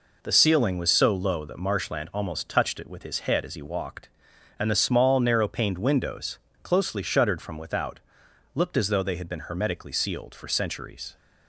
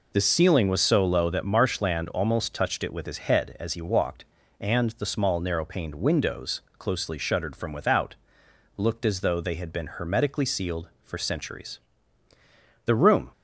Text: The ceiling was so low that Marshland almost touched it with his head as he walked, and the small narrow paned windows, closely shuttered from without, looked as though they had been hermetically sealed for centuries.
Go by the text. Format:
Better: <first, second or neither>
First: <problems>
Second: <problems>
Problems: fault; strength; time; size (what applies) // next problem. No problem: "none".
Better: first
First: none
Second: goes on to say "The room"; slight; from 12.8 s on; 0.46 s long